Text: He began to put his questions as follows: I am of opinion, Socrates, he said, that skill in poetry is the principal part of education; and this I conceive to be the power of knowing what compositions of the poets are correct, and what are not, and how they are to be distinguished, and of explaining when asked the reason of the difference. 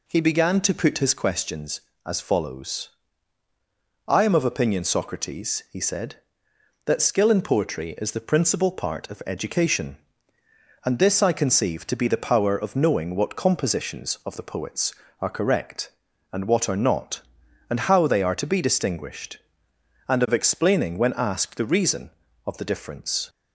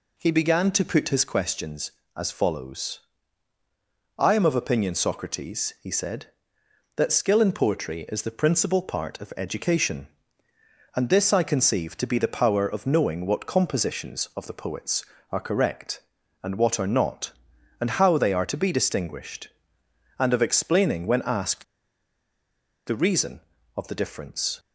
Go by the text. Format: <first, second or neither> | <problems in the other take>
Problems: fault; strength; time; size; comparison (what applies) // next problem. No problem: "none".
first | pauses between "asked" and "the"; at 21.6 s; 1.2 s long